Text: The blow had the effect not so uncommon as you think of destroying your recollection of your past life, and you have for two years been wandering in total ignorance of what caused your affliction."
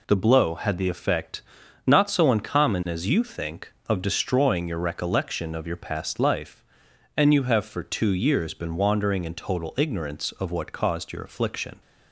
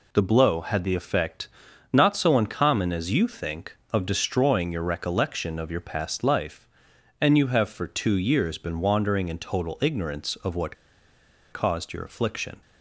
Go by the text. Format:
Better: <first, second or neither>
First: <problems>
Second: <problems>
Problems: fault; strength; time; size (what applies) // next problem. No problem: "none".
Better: first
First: pauses between "effect" and "not"; noticeable; at 1.4 s; 0.46 s long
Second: pauses between "effect" and "not"; noticeable; at 1.4 s; 0.46 s long // pauses between "what" and "caused"; noticeable; at 10.7 s; 0.77 s long